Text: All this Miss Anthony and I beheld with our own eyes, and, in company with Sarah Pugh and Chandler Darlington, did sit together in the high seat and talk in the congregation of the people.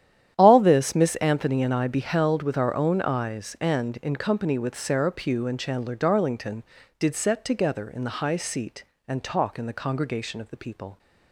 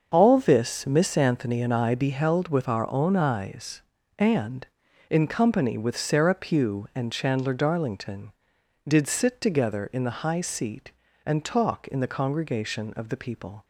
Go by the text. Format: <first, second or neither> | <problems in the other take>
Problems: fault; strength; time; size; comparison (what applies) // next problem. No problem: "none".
second | starts louder than the rest; strong; until 1.3 s; 10.5 dB; also in the second // says "set" for "sit"; at 7.1 s